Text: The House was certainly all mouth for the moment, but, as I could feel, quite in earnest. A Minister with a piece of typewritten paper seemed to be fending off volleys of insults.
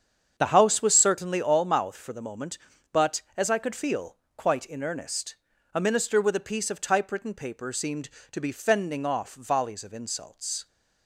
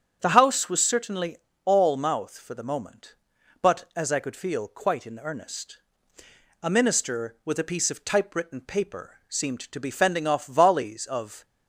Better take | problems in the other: first | starts louder than the rest; strong; until 1.2 s; 7.5 dB; strong in the first // pauses between "certainly" and "all"; slight; at 1.3 s; 0.26 s long // stops before "insults"; at 11.4 s

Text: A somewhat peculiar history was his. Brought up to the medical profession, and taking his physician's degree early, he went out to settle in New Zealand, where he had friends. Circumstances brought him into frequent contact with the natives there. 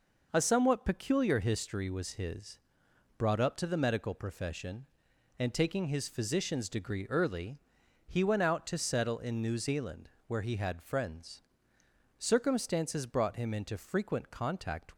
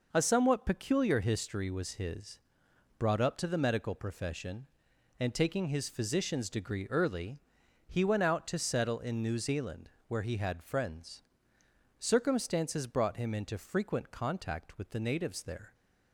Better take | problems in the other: second | stops before "with the natives there"; at 14.9 s

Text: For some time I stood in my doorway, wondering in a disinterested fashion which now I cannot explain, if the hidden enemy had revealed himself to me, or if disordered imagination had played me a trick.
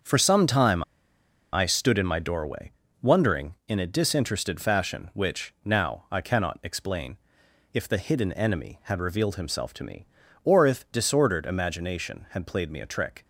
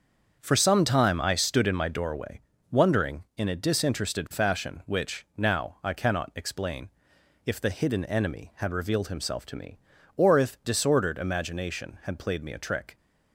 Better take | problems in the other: second | starts louder than the rest; until 1.7 s; 7 dB; also in the second // pauses between "time" and "I"; noticeable; at 0.8 s; 0.71 s long

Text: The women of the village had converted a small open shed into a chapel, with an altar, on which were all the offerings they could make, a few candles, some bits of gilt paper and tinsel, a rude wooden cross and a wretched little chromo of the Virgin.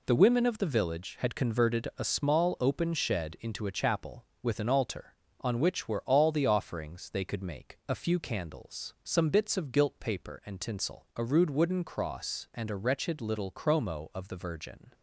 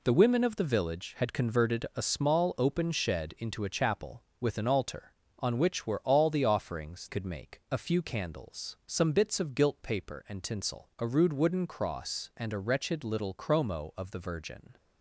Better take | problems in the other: first | skips "they"; at 7.0 s

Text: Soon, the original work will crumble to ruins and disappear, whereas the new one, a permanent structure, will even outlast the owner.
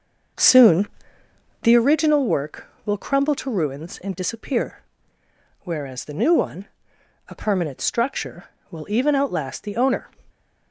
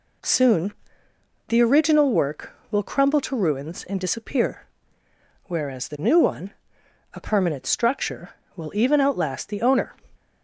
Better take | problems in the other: second | starts louder than the rest; noticeable; until 1.8 s; 6 dB

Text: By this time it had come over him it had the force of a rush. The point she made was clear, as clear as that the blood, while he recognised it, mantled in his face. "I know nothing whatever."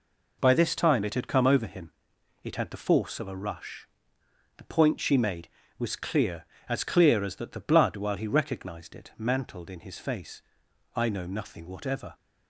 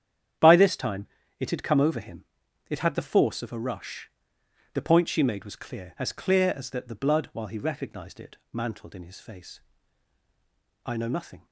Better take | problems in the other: first | starts louder than the rest; strong; until 1.7 s; 9.5 dB // pauses between "time" and "it"; slight; at 1.0 s; 0.34 s long // pauses between "him" and "it"; noticeable; at 2.2 s; 0.46 s long; noticeable in the first // stops before "whatever"; at 11.4 s

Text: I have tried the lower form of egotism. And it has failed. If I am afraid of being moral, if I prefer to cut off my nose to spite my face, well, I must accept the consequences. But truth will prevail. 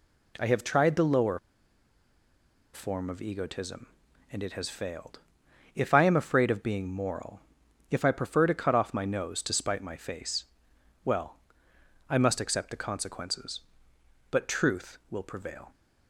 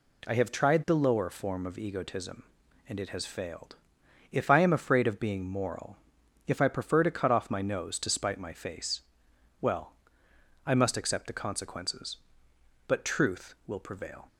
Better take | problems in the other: second | pauses between "lower" and "form"; strong; at 1.3 s; 1.3 s long

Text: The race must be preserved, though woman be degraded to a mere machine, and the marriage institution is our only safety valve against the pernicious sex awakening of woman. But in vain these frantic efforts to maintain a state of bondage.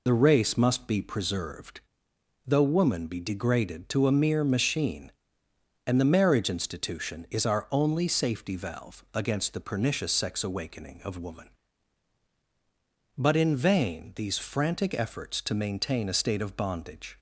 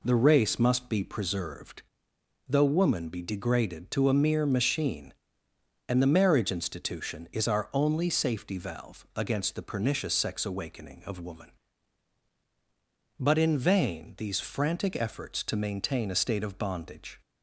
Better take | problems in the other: second | loses the start of "The"; at 0.0 s; 45 ms

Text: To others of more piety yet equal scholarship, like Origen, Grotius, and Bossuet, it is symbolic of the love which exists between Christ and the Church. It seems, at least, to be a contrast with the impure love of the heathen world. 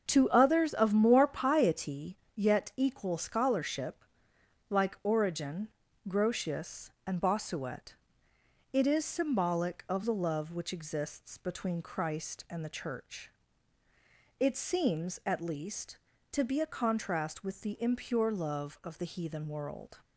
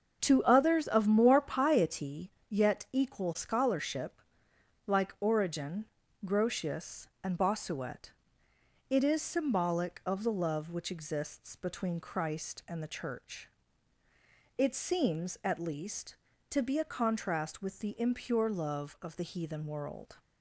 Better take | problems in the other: neither | starts louder than the rest; the same in both // pauses between "piety" and "yet"; slight; the same in both

